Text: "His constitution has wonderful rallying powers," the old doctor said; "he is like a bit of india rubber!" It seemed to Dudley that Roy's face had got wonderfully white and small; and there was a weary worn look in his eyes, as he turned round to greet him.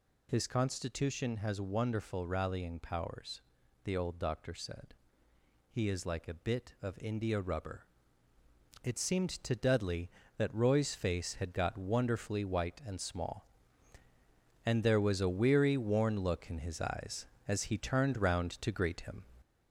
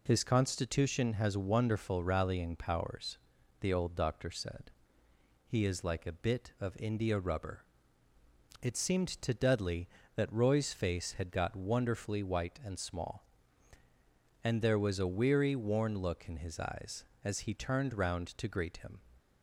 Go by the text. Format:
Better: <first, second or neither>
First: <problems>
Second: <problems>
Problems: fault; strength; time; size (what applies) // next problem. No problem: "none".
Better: second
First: gets louder; throughout; 4 dB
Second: none